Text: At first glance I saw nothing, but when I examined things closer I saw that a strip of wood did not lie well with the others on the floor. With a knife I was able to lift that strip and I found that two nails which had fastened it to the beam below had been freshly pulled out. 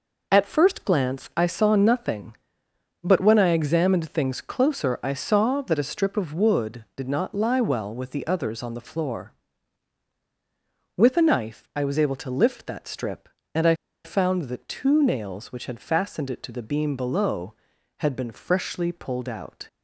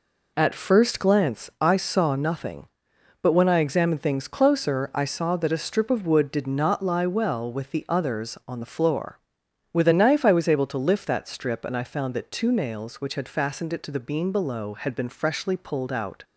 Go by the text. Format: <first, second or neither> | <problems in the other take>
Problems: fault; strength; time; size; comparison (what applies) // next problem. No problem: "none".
second | pauses between "I" and "found"; slight; at 13.7 s; 0.29 s long